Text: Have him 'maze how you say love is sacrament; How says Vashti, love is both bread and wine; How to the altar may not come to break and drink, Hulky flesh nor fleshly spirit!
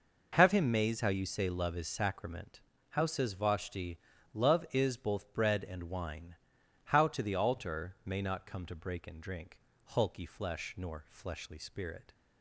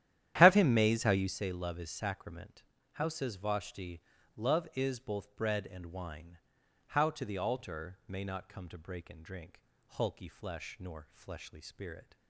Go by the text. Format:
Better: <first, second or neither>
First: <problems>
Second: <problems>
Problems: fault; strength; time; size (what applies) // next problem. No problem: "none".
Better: first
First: none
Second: starts louder than the rest; strong; until 1.5 s; 11.5 dB